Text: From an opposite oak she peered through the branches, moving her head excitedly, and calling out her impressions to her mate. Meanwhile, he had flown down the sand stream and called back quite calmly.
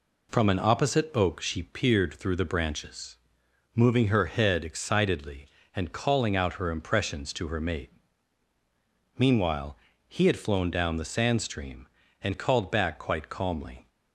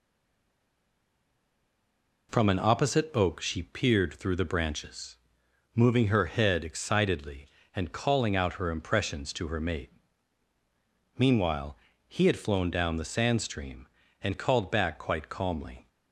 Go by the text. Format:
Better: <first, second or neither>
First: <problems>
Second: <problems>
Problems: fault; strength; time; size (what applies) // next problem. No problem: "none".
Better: first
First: none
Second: stays silent before the first word; until 2.2 s; 2.2 s long